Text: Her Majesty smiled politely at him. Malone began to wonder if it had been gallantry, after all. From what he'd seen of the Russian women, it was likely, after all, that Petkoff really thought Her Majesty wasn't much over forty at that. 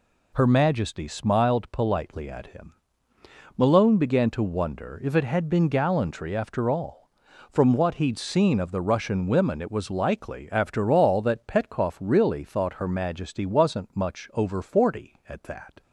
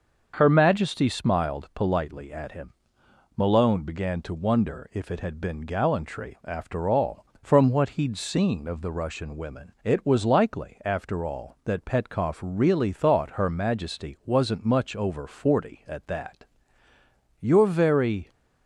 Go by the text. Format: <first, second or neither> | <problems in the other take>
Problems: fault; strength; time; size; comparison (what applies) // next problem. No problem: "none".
first | starts louder than the rest; until 1.3 s; 6.5 dB // goes on to say "You're very"; noticeable; from 17.4 s on; 0.90 s long